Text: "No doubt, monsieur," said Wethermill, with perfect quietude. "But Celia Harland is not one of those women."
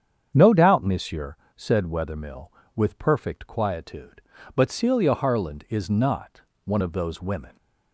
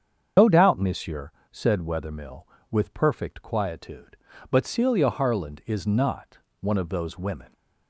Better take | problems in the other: first | loses the start of "No"; at 0.3 s; 75 ms // starts louder than the rest; strong; until 1.5 s; 7.5 dB; strong in the first // pauses between "not" and "one"; slight; at 6.3 s; 0.18 s long; slight in the first

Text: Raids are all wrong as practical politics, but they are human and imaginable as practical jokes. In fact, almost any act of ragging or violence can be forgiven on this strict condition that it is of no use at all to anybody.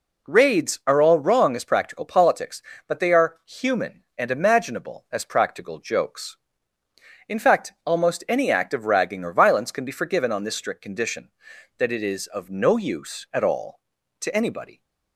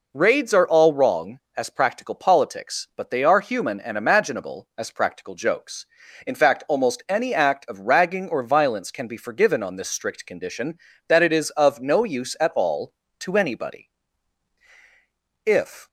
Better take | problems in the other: first | goes on to say "If"; slight; from 15.4 s on; 0.42 s long

